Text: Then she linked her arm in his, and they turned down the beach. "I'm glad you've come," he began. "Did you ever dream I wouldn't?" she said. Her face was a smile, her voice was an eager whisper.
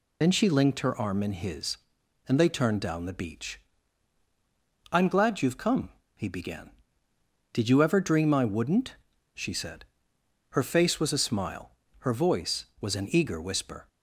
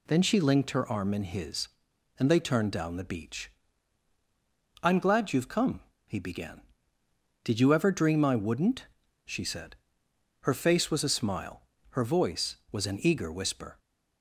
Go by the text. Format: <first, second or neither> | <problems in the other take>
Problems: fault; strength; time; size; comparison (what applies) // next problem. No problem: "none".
second | loses the start of "Then"; at 0.2 s; 55 ms